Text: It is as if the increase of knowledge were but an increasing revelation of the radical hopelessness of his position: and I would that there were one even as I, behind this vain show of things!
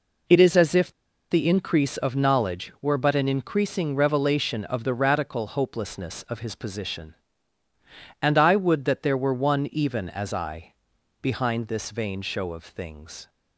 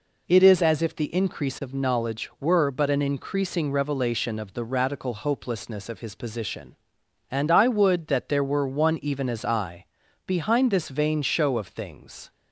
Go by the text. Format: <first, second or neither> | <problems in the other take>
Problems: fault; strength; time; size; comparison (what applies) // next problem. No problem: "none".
second | pauses between "if" and "the"; at 0.9 s; 0.40 s long